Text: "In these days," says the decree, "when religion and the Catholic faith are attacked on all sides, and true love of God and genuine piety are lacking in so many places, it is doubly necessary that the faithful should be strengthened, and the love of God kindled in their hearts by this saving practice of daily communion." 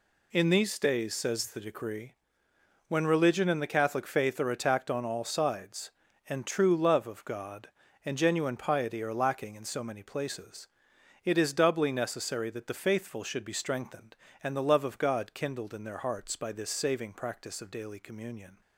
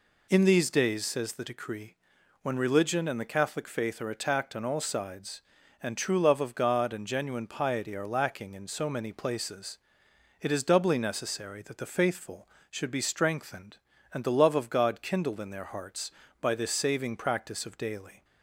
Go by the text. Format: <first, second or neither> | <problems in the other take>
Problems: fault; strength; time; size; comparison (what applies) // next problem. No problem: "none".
first | stops before "communion"; at 18.2 s